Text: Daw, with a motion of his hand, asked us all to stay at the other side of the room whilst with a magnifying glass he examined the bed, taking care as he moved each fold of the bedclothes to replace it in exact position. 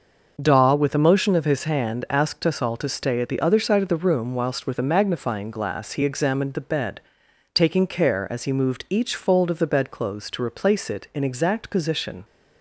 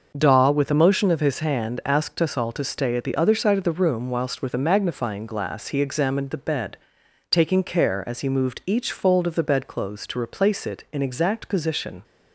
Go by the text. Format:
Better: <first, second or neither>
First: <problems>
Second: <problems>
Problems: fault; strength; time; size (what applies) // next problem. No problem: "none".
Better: neither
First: starts louder than the rest; noticeable; until 1.4 s; 6 dB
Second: starts louder than the rest; noticeable; until 1.1 s; 6 dB